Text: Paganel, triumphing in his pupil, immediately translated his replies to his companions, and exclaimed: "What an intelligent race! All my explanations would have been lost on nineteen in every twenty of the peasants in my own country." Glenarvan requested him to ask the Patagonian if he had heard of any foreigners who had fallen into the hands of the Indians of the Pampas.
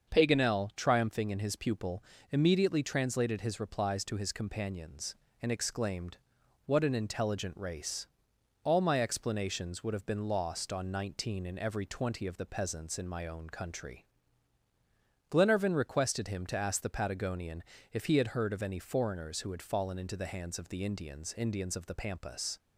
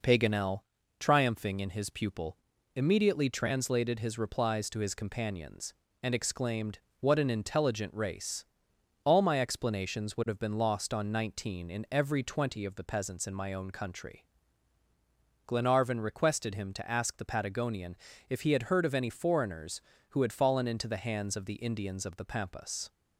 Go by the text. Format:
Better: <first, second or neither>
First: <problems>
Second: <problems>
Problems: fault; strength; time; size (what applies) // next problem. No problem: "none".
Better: second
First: starts louder than the rest; until 1.1 s; 6.5 dB // pauses between "Patagonian" and "if"; slight; at 17.6 s; 0.30 s long // says "Indians" twice; at 21.3 s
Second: pauses between "Patagonian" and "if"; slight; at 17.9 s; 0.32 s long